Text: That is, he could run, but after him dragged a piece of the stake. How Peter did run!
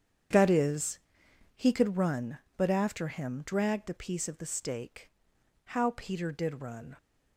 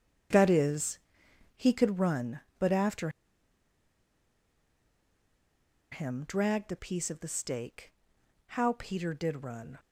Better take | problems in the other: first | starts louder than the rest; strong; until 1.9 s; 8.5 dB; strong in the first // pauses between "after" and "him"; strong; at 3.0 s; 2.8 s long

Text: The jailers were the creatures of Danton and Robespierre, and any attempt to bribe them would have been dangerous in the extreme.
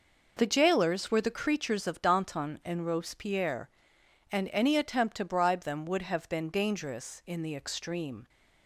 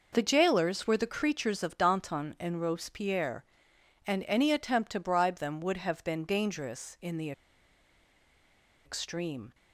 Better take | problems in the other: first | pauses between "the" and "extreme"; strong; at 7.3 s; 1.5 s long

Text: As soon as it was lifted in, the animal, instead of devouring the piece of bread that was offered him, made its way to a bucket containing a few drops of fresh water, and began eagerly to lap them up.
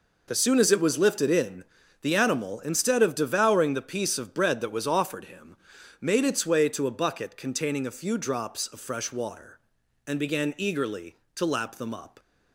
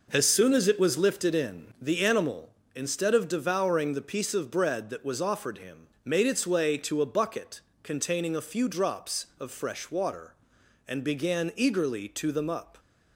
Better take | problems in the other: first | pauses between "bucket" and "containing"; slight; at 7.6 s; 0.22 s long // skips "lap"; at 12.3 s

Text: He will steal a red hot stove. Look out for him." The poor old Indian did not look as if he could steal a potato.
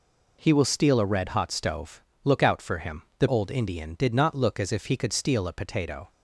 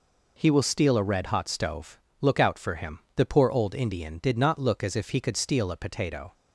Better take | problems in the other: second | skips "poor"; at 3.2 s

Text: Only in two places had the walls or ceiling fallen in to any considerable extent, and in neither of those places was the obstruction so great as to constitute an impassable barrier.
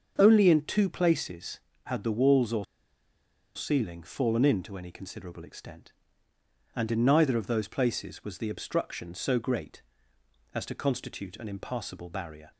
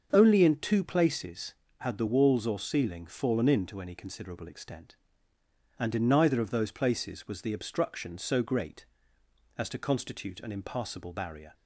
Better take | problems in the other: second | starts louder than the rest; until 1.1 s; 6.5 dB; also in the second // pauses between "or" and "ceiling"; noticeable; at 2.6 s; 0.90 s long

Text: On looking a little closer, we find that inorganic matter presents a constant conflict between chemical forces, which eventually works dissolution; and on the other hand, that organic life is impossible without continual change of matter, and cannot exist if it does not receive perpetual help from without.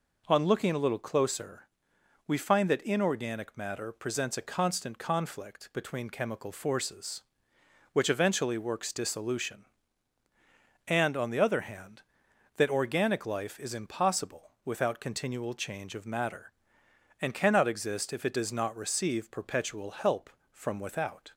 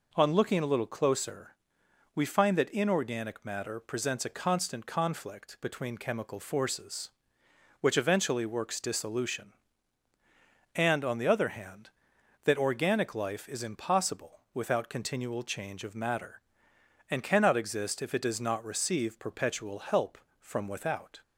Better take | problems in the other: neither | none

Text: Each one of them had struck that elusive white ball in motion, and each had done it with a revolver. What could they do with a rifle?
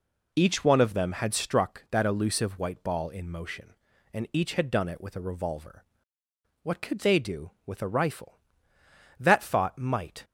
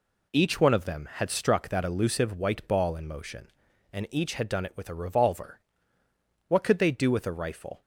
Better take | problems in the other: second | goes on to say "That thought might"; noticeable; from 9.1 s on; 1.0 s long

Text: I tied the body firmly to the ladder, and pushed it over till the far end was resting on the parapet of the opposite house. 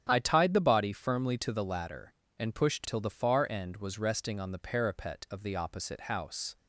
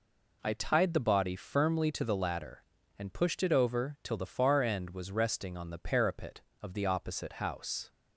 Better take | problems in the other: second | starts louder than the rest; strong; until 1.1 s; 9 dB // skips "it over"; at 2.8 s

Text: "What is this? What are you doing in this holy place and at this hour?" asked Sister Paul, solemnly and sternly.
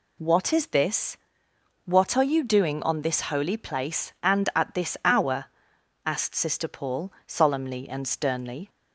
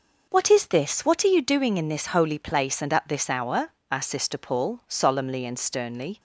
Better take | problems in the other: second | says "on" for "in"; at 2.8 s

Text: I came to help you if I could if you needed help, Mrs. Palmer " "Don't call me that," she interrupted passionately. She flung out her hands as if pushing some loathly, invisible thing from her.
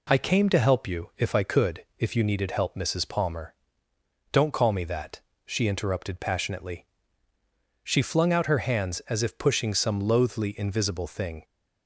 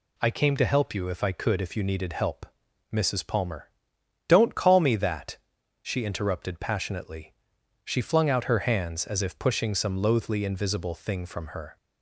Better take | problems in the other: second | stops before "from her"; at 11.4 s

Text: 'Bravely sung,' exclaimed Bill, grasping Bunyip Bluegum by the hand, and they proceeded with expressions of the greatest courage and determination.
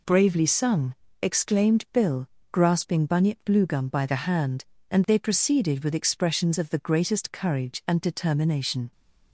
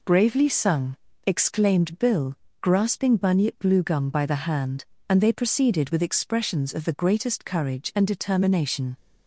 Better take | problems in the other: neither | none

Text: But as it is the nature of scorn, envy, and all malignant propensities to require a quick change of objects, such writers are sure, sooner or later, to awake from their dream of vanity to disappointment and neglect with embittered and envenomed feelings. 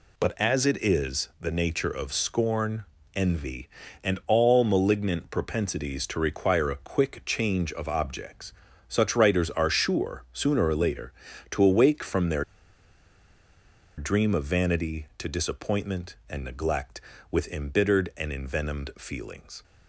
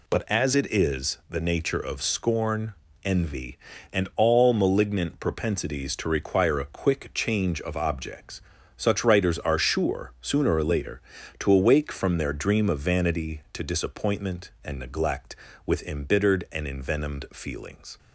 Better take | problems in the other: second | pauses between "their" and "dream"; strong; at 12.4 s; 1.5 s long

